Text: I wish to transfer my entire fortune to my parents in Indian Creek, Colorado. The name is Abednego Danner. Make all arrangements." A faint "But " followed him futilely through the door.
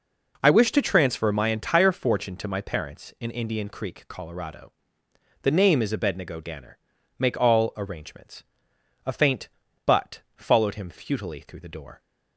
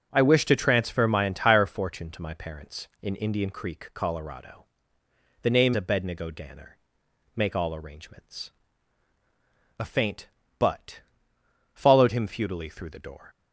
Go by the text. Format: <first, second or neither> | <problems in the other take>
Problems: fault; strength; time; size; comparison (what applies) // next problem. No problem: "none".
first | starts louder than the rest; strong; until 1.1 s; 7.5 dB // skips "is"; at 5.7 s